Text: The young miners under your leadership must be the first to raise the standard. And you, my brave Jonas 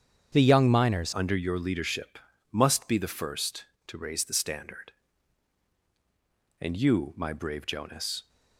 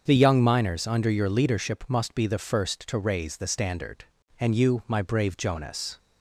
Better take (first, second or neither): second